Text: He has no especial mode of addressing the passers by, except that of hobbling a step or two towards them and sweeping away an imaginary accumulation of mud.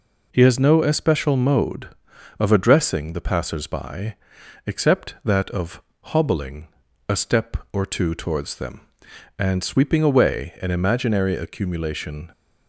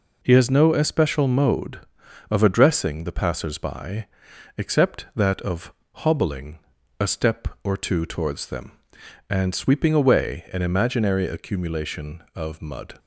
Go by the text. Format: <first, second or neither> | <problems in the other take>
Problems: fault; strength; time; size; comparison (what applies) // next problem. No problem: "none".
second | pauses between "of" and "hobbling"; slight; at 5.8 s; 0.24 s long; slight in the second // pauses between "hobbling" and "a"; at 6.6 s; 0.42 s long; also in the second // stops before "of mud"; at 12.3 s